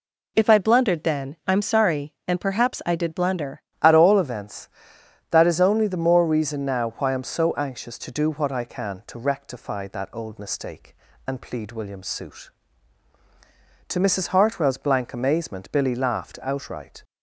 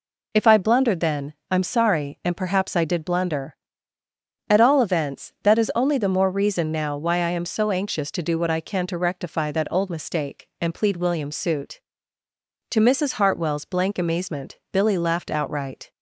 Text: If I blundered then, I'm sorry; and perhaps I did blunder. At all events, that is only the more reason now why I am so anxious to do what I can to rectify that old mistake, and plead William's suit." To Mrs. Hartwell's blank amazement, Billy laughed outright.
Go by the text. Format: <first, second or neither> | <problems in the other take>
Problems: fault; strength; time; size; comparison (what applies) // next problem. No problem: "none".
second | changes voice at "At"; from 3.8 s on; 13.2 s long